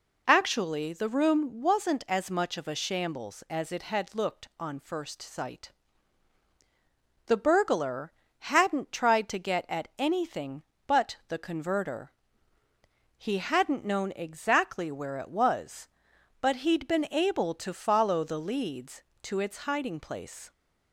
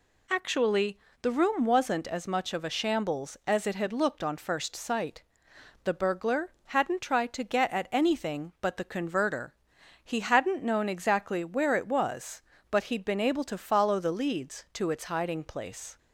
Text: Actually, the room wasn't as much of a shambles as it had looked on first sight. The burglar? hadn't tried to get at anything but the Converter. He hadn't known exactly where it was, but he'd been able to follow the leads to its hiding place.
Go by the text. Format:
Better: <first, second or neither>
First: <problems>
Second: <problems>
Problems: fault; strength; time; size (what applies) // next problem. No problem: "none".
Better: neither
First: none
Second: none